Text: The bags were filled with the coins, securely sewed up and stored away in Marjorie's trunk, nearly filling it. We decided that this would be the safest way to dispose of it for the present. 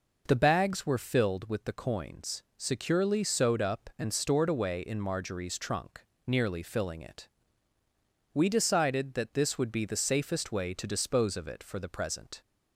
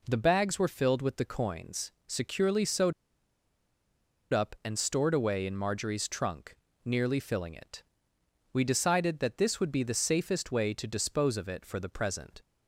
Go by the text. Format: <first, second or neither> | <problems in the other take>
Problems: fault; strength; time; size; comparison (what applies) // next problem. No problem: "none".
first | pauses between "sewed" and "up"; strong; at 2.9 s; 1.3 s long